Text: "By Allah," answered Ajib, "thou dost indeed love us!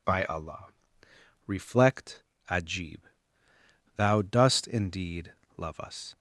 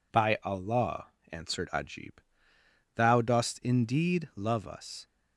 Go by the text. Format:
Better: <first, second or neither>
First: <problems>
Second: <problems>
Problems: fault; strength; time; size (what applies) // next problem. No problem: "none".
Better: second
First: says "reflect" for "answered"; at 1.4 s // pauses between "indeed" and "love"; slight; at 5.3 s; 0.22 s long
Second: none